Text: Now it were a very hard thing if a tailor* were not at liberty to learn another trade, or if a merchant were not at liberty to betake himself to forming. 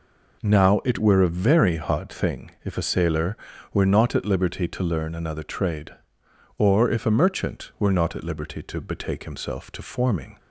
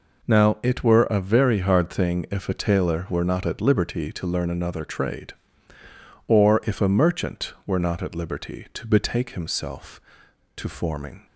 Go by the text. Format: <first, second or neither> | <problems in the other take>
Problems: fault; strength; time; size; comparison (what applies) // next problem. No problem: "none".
second | says "sailor" for "tailor"; at 2.8 s